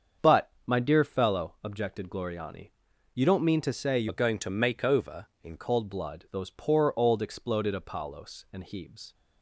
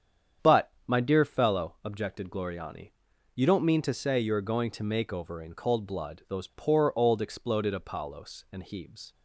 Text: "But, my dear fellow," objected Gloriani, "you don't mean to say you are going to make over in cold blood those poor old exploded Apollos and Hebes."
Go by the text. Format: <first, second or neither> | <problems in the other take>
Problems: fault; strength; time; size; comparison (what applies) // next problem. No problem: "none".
second | starts louder than the rest; strong; until 1.3 s; 7 dB; strong in the second // changes voice from "are" to "in"; from 4.0 to 5.5 s; 1.5 s long